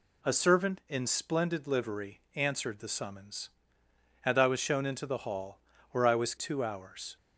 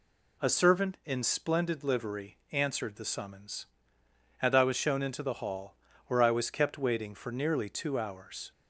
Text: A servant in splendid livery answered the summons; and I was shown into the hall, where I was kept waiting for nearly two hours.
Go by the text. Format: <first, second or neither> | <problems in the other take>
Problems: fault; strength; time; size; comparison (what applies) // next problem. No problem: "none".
second | skips "kept waiting for nearly"; at 6.3 s